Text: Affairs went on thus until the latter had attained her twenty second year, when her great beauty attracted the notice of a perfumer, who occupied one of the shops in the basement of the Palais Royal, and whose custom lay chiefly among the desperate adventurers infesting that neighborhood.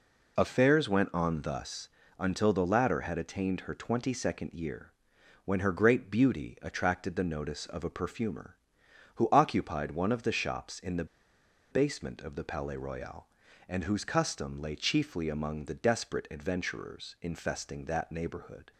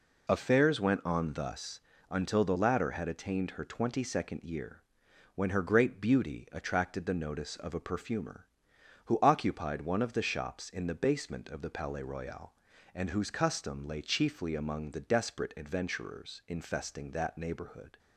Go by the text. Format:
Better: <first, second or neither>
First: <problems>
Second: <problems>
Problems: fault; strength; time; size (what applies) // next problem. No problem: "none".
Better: second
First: pauses between "thus" and "until"; slight; at 1.8 s; 0.30 s long // pauses between "the" and "basement"; noticeable; at 11.0 s; 0.65 s long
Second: pauses between "thus" and "until"; slight; at 1.7 s; 0.30 s long